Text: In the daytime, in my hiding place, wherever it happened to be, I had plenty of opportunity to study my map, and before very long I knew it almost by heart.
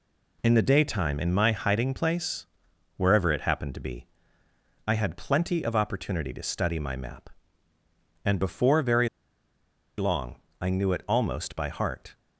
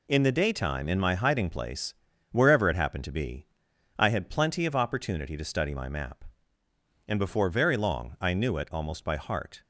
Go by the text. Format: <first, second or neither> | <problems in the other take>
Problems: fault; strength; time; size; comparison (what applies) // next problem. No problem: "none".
second | pauses between "very" and "long"; noticeable; at 9.0 s; 0.90 s long // pauses between "long" and "I"; slight; at 10.3 s; 0.22 s long